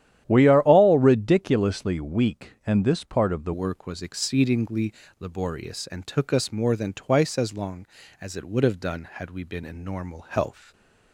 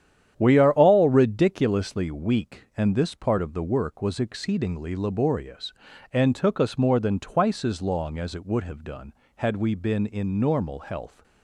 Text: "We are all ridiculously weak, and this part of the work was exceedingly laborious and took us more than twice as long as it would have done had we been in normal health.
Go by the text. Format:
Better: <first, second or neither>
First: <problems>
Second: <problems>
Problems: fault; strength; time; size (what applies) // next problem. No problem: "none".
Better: second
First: starts louder than the rest; strong; until 1.2 s; 11.5 dB // changes voice at "work"; from 3.5 s on; 7.2 s long // pauses between "exceedingly" and "laborious"; slight; at 4.9 s; 0.26 s long // stays silent after the last word; slight; from 10.6 s on; 0.5 s long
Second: starts louder than the rest; strong; until 1.3 s; 10 dB